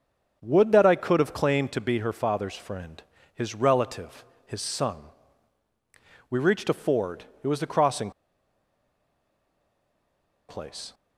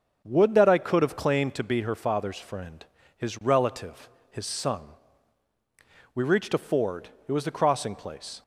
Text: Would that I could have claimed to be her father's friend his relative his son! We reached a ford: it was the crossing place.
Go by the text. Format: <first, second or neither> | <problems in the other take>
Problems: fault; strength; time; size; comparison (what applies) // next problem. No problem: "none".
second | starts louder than the rest; until 1.4 s; 6.5 dB; also in the second // pauses between "friend" and "his"; slight; at 3.0 s; 0.32 s long; slight in the second // pauses between "relative" and "his"; slight; at 4.2 s; 0.22 s long; slight in the second // pauses between "crossing" and "place"; strong; at 8.0 s; 2.3 s long